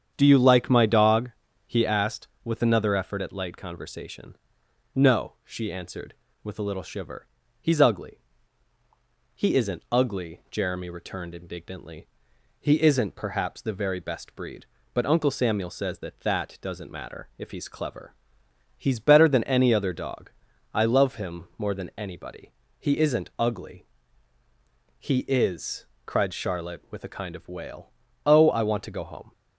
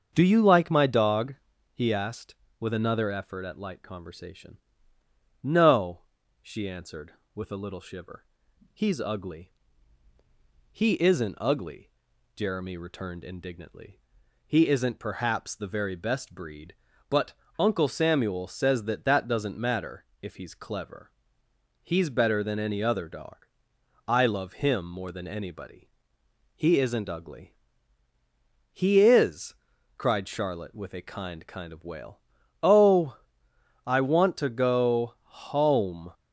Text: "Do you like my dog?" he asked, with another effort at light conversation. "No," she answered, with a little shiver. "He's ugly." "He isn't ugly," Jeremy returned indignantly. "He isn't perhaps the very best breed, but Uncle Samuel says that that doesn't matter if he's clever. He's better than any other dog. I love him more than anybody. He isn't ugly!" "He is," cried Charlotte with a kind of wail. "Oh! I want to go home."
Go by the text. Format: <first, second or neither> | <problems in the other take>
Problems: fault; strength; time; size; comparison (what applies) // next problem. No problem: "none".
first | starts louder than the rest; until 1.1 s; 7 dB; strong in the first // pauses between "but" and "Uncle"; slight; at 17.3 s; 0.24 s long // pauses between "matter" and "if"; slight; at 20.0 s; 0.16 s long // says "kind" twice; at 31.4 s